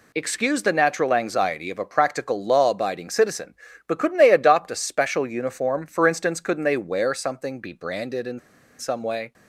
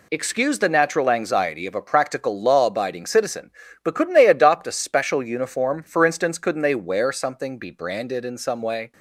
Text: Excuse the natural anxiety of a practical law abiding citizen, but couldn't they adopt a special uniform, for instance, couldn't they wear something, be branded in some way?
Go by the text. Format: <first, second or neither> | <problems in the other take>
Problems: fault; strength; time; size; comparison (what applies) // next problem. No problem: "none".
second | pauses between "in" and "some"; at 8.3 s; 0.40 s long